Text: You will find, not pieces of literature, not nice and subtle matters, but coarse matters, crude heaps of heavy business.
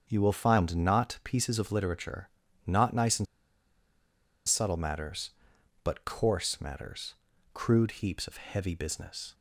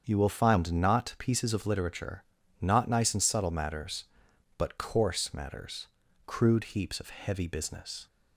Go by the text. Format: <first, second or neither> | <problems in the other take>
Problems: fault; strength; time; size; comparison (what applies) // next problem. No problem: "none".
second | starts louder than the rest; strong; until 1.0 s; 7.5 dB; strong in the second // pauses between "and" and "subtle"; at 3.2 s; 1.2 s long